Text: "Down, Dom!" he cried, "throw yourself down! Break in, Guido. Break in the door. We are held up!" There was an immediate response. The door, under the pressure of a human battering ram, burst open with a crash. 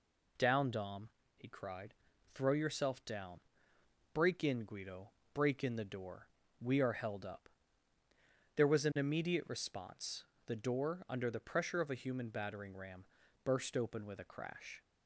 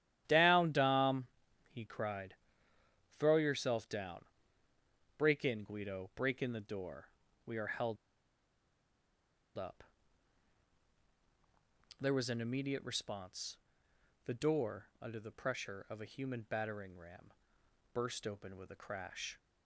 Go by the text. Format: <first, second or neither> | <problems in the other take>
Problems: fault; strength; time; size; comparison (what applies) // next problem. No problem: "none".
first | starts louder than the rest; strong; until 1.2 s; 12 dB // pauses between "held" and "up"; strong; at 7.9 s; 1.6 s long